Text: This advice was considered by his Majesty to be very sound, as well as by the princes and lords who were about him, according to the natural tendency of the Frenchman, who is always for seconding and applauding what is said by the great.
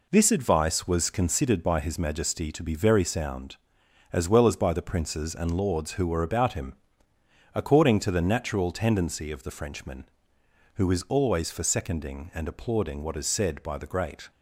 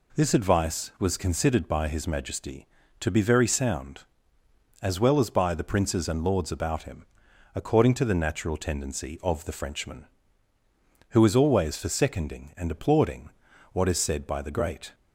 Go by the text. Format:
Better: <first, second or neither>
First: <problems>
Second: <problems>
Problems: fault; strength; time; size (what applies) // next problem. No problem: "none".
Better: first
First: none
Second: skips "who were"; at 6.4 s // pauses between "applauding" and "what"; at 13.2 s; 0.42 s long